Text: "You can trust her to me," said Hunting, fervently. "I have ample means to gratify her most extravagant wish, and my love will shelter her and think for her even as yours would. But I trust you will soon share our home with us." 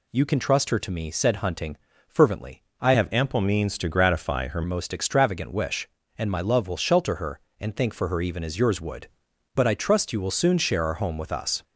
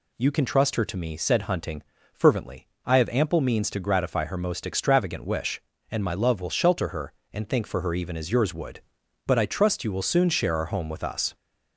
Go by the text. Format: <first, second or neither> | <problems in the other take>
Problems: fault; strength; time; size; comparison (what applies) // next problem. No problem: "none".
second | changes voice from "have" to "her"; from 2.9 to 4.6 s; 1.7 s long